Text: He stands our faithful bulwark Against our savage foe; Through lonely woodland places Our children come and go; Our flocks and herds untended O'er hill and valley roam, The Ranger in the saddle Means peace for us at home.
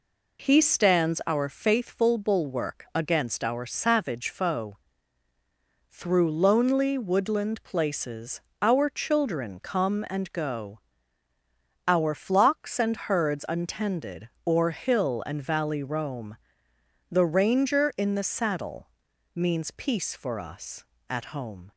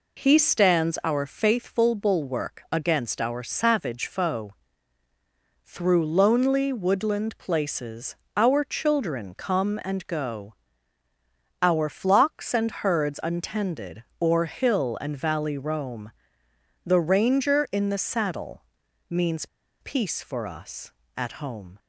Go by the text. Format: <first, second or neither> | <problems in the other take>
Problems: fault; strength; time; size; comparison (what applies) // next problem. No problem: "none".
first | pauses between "places" and "Our"; slight; at 8.1 s; 0.20 s long; slight in the first // pauses between "untended" and "O'er"; slight; at 14.0 s; 0.18 s long; slight in the first // pauses between "saddle" and "Means"; at 18.6 s; 0.44 s long; also in the first // pauses between "Means" and "peace"; slight; at 19.4 s; 0.35 s long